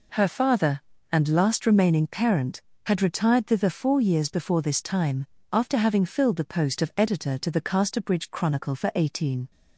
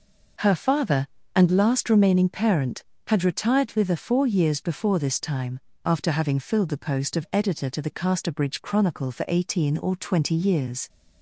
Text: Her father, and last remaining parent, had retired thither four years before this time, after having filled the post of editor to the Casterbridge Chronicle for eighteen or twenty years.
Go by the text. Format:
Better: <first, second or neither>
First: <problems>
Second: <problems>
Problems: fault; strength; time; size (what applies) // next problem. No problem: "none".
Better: second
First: stops before "or twenty years"; at 9.5 s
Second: none